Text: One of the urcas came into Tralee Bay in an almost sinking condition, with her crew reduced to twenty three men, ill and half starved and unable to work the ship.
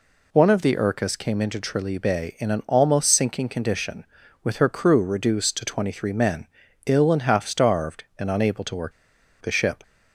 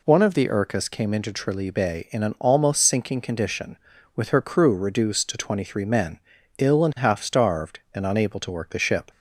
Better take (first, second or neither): second